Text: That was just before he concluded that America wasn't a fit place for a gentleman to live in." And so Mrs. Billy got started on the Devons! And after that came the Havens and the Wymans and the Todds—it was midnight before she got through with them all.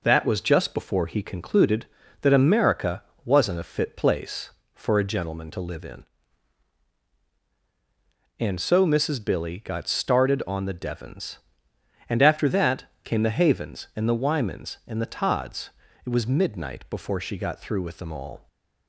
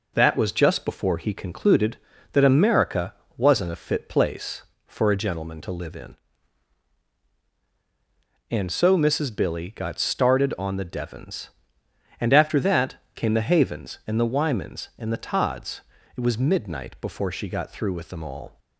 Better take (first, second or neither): neither